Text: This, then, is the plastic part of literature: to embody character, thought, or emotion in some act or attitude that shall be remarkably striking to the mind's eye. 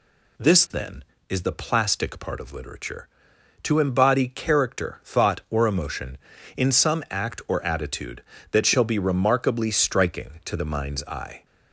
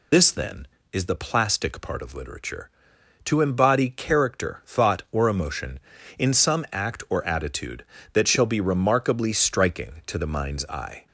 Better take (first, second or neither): first